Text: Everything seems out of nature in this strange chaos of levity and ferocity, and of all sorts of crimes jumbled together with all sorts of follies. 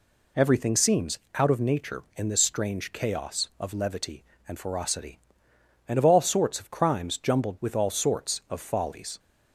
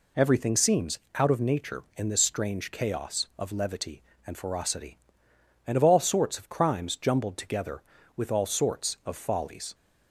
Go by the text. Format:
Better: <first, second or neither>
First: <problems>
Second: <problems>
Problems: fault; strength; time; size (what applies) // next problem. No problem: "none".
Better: second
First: pauses between "seems" and "out"; slight; at 1.1 s; 0.16 s long // skips "together"; at 7.5 s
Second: pauses between "seems" and "out"; slight; at 0.9 s; 0.16 s long